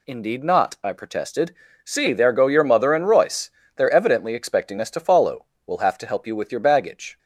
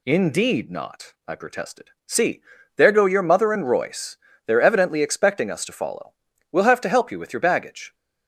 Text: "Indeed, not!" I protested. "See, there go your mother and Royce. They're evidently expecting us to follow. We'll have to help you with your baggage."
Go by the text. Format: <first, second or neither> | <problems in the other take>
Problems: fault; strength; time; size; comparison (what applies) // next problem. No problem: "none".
neither | none